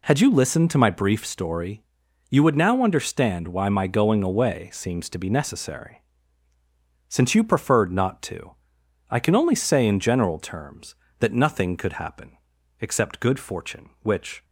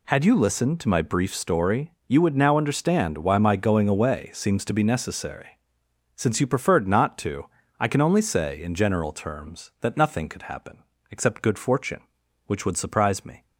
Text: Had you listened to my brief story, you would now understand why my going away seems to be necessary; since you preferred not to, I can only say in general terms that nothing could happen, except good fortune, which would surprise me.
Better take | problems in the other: second | stops before "would surprise me"; at 14.4 s

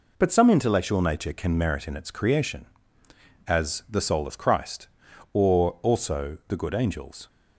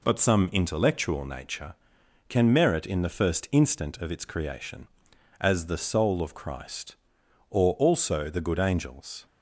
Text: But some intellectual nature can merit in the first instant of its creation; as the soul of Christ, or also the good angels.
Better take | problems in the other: second | skips "the first instant of"; at 1.9 s

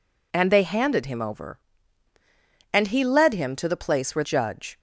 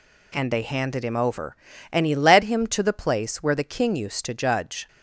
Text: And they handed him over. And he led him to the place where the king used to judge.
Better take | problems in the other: second | skips "the king used to"; at 4.2 s

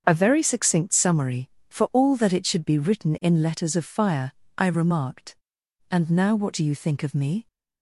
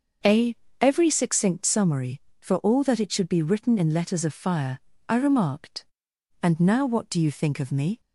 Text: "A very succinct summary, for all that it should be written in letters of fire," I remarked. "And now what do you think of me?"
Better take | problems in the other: first | starts louder than the rest; until 1.5 s; 6 dB; also in the first // says "every" for "very"; at 0.8 s

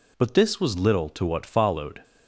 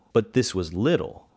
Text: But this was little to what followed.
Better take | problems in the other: first | stops before "to what followed"; at 1.2 s

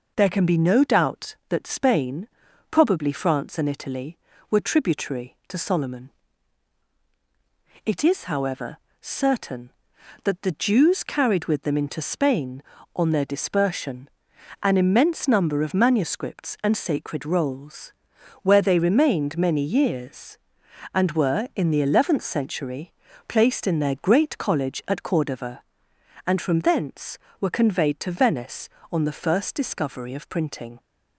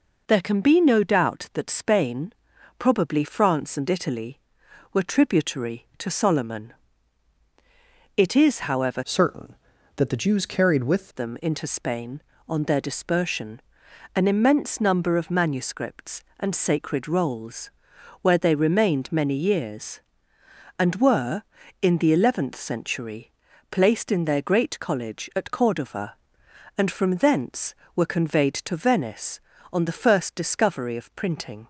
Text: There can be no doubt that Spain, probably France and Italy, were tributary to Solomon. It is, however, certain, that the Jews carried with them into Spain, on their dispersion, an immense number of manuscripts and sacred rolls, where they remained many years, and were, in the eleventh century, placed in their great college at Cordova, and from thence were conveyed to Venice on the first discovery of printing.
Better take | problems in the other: first | changes voice from "certain" to "with"; from 9.0 to 11.0 s; 2.0 s long

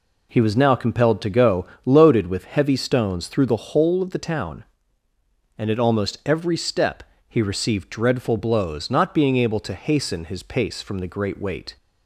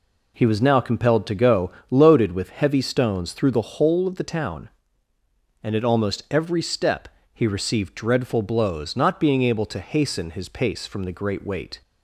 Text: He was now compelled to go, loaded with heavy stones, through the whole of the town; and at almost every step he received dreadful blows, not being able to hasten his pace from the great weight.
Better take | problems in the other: neither | pauses between "step" and "he"; slight; the same in both

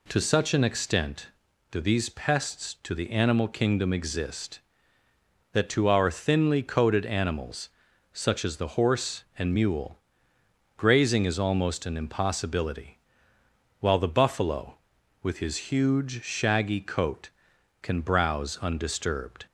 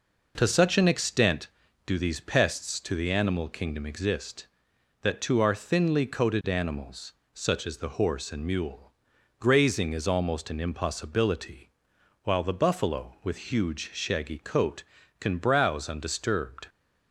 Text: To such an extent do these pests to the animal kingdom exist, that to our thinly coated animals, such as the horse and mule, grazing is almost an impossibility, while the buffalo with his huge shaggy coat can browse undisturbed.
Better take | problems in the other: first | skips "his"; at 13.5 s

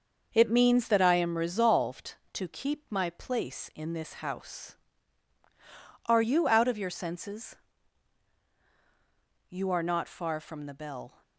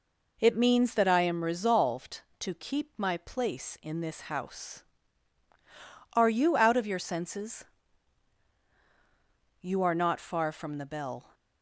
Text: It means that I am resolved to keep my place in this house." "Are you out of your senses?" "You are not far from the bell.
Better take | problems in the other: second | gets quieter; strong; throughout; 7 dB

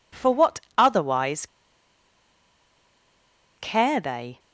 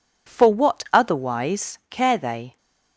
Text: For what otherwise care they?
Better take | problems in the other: second | pauses between "what" and "otherwise"; slight; at 0.6 s; 0.16 s long // pauses between "otherwise" and "care"; strong; at 1.4 s; 2.1 s long

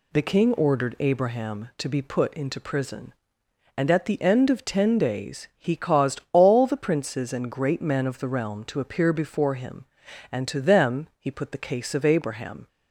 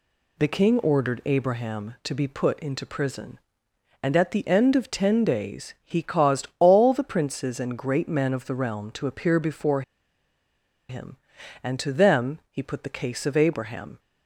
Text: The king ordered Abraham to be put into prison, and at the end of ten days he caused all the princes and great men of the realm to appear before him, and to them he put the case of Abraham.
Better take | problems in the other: first | pauses between "before" and "him"; at 9.8 s; 1.0 s long

